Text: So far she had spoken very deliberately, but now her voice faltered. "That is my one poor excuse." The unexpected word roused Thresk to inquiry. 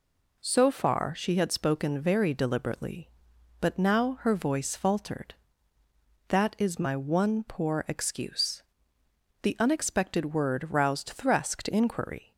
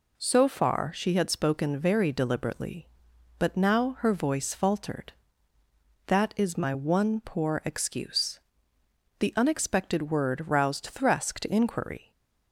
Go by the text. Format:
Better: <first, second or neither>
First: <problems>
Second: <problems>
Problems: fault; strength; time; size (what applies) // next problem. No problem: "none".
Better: neither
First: none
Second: none